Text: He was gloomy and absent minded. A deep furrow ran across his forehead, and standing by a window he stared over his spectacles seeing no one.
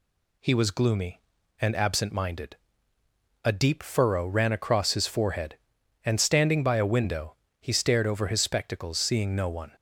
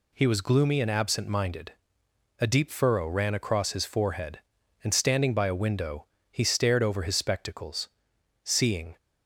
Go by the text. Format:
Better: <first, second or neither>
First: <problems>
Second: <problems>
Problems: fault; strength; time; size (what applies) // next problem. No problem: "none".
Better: first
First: pauses between "window" and "he"; slight; at 7.3 s; 0.24 s long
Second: pauses between "window" and "he"; slight; at 6.0 s; 0.24 s long // pauses between "spectacles" and "seeing"; noticeable; at 7.8 s; 0.60 s long // stops before "no one"; at 8.9 s